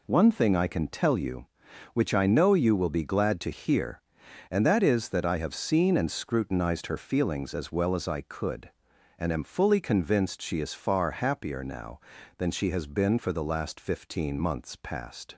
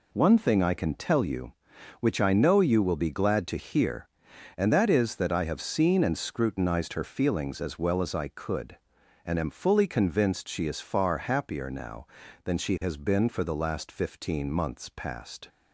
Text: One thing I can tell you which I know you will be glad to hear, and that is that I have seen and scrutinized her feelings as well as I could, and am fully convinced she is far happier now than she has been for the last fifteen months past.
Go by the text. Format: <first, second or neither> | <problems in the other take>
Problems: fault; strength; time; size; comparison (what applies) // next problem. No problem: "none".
neither | none